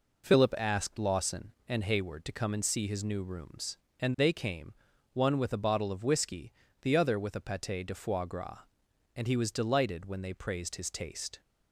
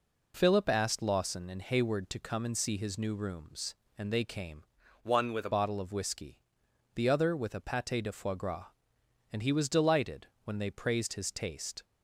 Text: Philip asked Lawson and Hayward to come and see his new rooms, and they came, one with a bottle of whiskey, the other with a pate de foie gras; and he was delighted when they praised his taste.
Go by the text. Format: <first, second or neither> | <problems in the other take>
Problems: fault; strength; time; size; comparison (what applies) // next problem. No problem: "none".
first | changes voice from "one" to "a"; from 5.0 to 5.5 s; 0.5 s long // pauses between "delighted" and "when"; slight; at 10.2 s; 0.18 s long